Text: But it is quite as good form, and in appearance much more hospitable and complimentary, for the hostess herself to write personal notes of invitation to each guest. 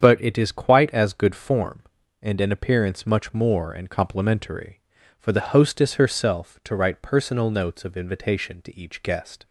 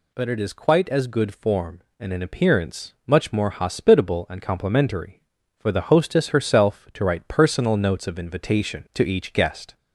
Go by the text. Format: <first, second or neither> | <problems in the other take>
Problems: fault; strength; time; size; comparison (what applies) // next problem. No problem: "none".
second | starts louder than the rest; strong; until 1.0 s; 8 dB // skips "hospitable"; at 3.7 s